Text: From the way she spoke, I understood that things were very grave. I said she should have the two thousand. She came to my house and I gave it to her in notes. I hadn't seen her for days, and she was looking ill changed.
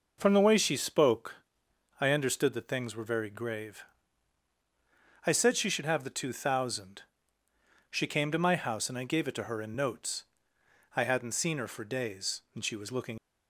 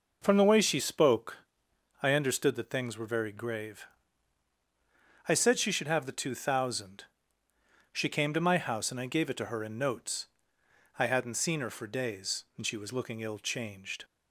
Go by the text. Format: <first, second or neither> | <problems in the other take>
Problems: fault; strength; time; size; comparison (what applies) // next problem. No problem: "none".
second | stops before "ill changed"; at 13.1 s